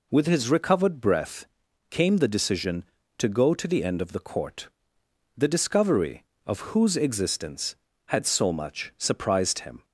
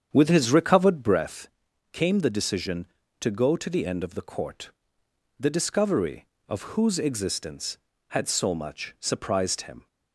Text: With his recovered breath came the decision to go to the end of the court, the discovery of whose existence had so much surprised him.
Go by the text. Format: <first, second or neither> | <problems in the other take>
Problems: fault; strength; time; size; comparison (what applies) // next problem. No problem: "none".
first | starts louder than the rest; strong; until 1.3 s; 8 dB // pauses between "breath" and "came"; at 1.4 s; 0.42 s long; also in the first